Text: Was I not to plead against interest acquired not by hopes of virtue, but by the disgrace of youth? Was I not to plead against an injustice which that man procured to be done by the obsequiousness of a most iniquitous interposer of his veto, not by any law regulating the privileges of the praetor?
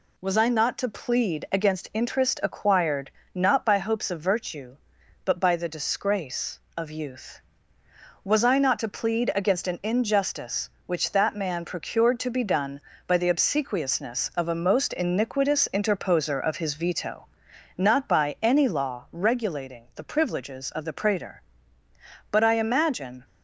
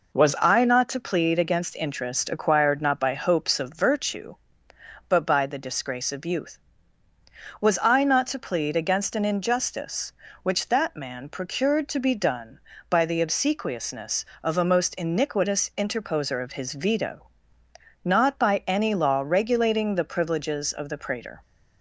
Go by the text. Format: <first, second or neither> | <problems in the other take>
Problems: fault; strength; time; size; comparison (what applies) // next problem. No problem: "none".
second | pauses between "acquired" and "not"; slight; at 3.1 s; 0.24 s long // goes on to say "But I imagine"; noticeable; from 22.3 s on; 0.94 s long